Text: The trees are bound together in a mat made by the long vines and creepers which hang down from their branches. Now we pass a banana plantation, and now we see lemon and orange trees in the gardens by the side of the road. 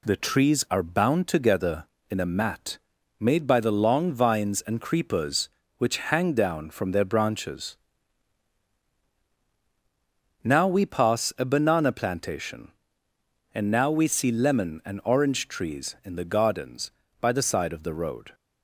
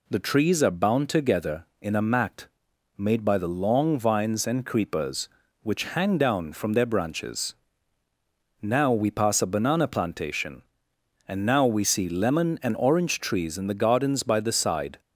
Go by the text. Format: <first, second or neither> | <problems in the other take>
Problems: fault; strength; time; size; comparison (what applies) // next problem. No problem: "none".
first | pauses between "mat" and "made"; noticeable; at 2.4 s; 0.50 s long; also in the first // stops before "of the road"; at 14.9 s